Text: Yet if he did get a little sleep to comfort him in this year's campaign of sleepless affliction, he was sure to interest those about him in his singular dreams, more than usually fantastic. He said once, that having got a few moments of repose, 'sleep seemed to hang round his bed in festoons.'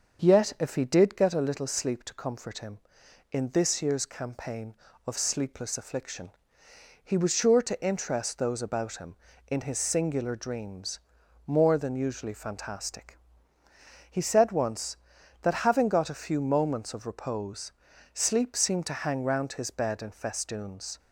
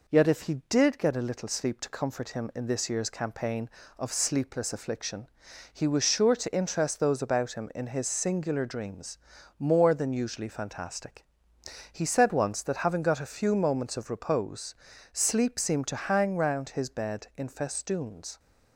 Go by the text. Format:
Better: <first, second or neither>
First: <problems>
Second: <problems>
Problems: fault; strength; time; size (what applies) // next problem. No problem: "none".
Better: second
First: starts louder than the rest; until 1.3 s; 6.5 dB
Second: none